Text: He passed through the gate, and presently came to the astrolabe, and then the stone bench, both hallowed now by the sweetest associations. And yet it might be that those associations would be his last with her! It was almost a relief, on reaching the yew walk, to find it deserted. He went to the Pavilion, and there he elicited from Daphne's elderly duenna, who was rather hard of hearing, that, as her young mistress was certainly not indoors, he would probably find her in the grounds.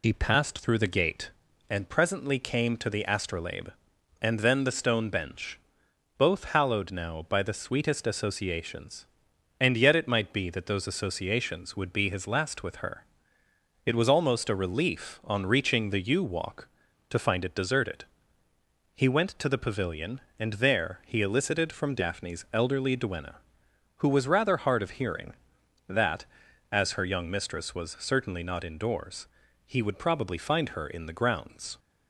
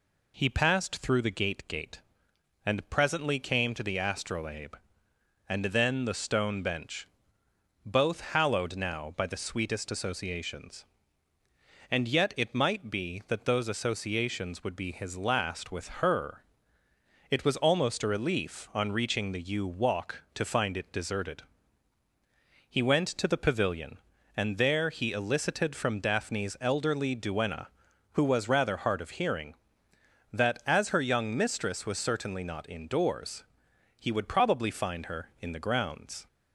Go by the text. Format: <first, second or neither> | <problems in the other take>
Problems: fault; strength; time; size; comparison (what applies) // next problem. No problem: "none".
first | says "gate" twice; at 1.6 s // pauses between "with" and "her"; slight; at 15.8 s; 0.16 s long